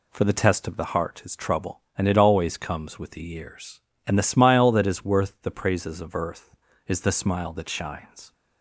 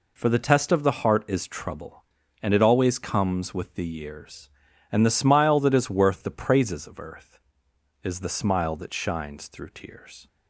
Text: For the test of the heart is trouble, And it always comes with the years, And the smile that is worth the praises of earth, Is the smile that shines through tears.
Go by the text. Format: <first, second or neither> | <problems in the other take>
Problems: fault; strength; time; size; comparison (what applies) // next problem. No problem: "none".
second | stops before "through tears"; at 8.3 s